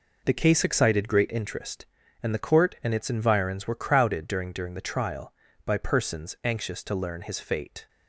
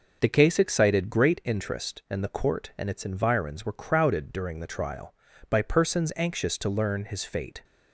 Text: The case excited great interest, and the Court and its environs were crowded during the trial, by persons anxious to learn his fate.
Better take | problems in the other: second | says "during" twice; at 4.5 s

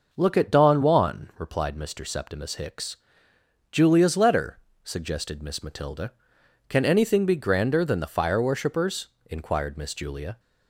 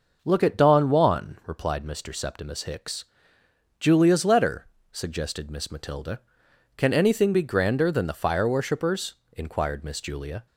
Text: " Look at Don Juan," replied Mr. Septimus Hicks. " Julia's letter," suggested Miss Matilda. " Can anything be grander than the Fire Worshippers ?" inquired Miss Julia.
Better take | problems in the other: neither | none

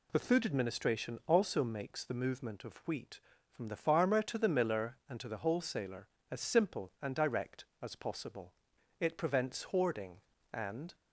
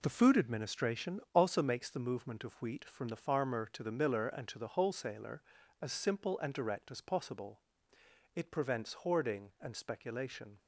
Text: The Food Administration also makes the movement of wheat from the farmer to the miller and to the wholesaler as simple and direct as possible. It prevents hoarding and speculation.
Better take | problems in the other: second | stops before "speculation"; at 10.9 s

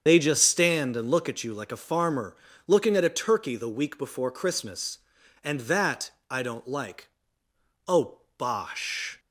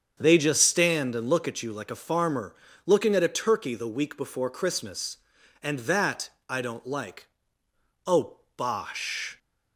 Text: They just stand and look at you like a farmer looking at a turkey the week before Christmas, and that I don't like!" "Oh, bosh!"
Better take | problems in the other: second | loses the start of "They"; at 0.0 s; 65 ms // starts louder than the rest; strong; until 1.0 s; 7.5 dB; strong in the second // pauses between "farmer" and "looking"; slight; at 2.3 s; 0.32 s long; slight in the second // pauses between "that" and "I"; slight; at 6.1 s; 0.18 s long; slight in the second

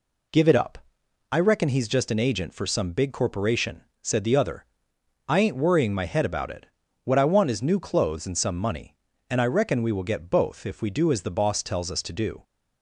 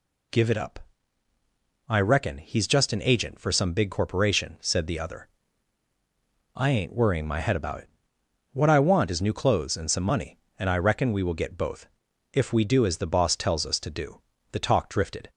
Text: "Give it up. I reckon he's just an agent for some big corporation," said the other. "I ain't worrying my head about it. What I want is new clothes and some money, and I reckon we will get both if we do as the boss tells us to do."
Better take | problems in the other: first | pauses between "both" and "if"; noticeable; at 11.8 s; 0.46 s long // goes on to say "The talk drifted"; noticeable; from 14.4 s on; 0.80 s long

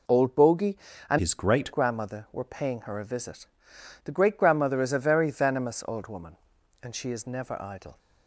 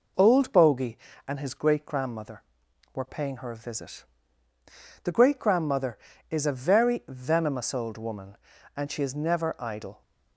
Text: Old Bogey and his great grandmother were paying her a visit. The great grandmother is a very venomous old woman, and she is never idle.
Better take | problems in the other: second | changes voice from "his" to "great"; from 1.1 to 1.7 s; 0.6 s long

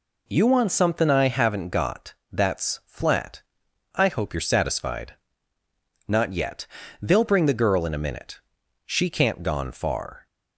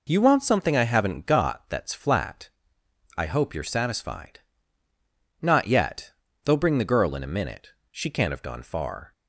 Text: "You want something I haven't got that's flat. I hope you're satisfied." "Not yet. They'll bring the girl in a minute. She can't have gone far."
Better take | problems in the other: second | pauses between "got" and "that's"; slight; at 2.1 s; 0.18 s long // skips "have"; at 9.4 s

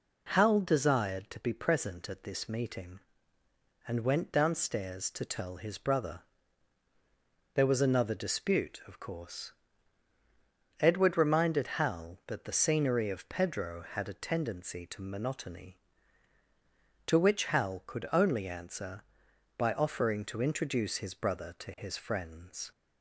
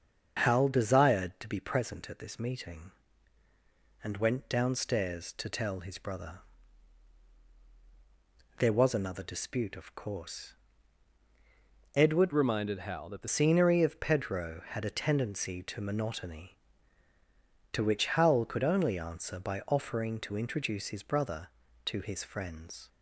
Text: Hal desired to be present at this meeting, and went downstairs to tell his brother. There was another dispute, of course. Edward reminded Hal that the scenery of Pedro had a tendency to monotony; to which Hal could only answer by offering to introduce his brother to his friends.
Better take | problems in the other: first | starts louder than the rest; until 1.5 s; 7 dB // changes voice from "reminded" to "the"; from 12.3 to 13.2 s; 0.9 s long

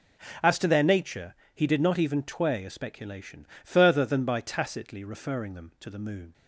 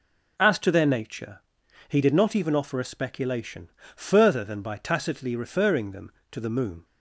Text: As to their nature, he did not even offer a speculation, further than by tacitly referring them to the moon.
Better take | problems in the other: second | says "tway" for "offer"; at 2.2 s

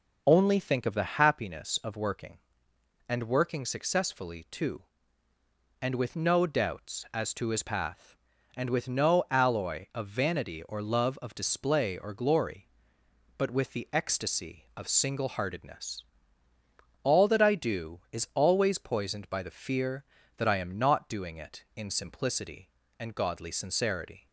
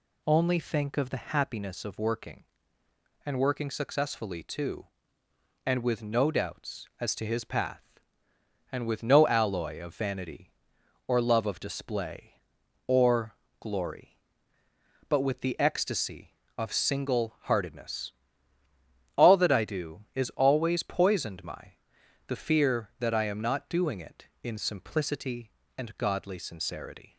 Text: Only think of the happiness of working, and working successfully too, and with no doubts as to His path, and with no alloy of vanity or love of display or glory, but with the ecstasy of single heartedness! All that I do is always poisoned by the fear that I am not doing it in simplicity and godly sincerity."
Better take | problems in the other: first | pauses between "or" and "glory"; slight; at 13.3 s; 0.26 s long // says "my" for "by"; at 21.4 s

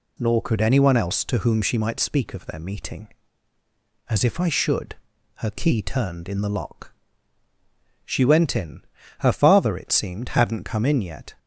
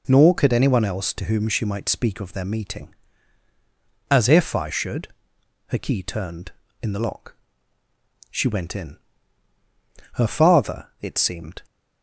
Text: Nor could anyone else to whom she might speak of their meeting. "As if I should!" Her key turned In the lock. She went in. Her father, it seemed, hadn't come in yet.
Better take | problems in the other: first | stops before "hadn't come in yet"; at 11.6 s

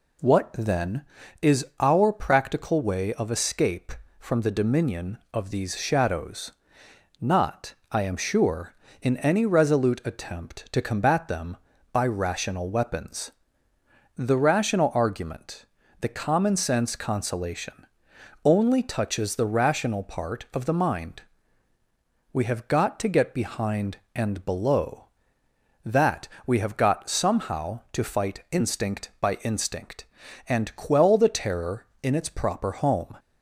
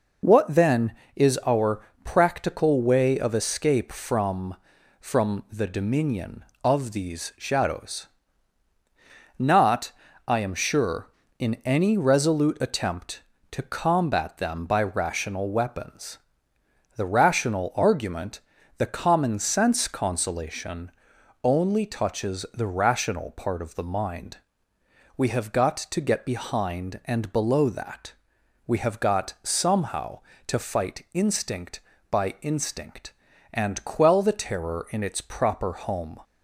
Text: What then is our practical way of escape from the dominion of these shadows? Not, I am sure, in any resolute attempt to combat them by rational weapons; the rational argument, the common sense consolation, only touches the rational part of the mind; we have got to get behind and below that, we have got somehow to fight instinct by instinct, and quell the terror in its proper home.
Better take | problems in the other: first | pauses between "our" and "practical"; slight; at 1.8 s; 0.18 s long // says "from" twice; at 4.9 s

